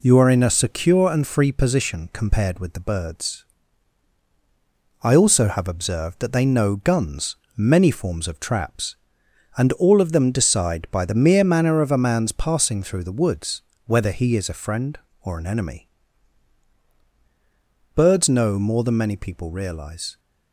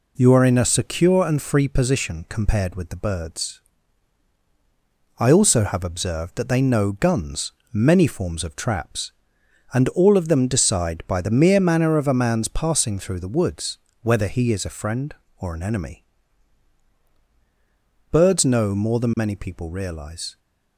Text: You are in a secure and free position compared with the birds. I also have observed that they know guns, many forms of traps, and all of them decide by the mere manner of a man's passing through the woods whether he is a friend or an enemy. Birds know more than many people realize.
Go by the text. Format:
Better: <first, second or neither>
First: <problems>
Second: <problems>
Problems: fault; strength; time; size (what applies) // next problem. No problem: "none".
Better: neither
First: pauses between "woods" and "whether"; slight; at 13.6 s; 0.26 s long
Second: pauses between "woods" and "whether"; slight; at 13.7 s; 0.26 s long